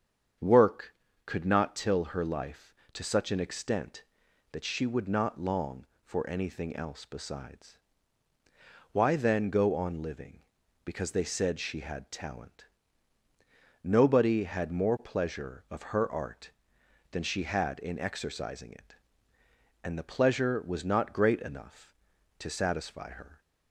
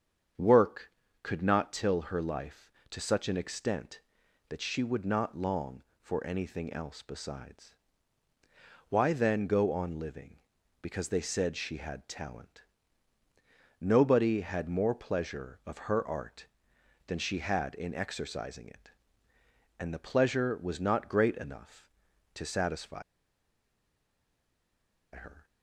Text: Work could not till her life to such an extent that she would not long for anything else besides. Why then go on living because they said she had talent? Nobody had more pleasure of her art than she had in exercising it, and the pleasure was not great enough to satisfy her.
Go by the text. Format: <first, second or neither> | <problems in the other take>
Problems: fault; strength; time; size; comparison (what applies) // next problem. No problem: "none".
first | starts louder than the rest; strong; until 1.6 s; 7.5 dB; strong in the first // pauses between "satisfy" and "her"; strong; at 23.0 s; 2.1 s long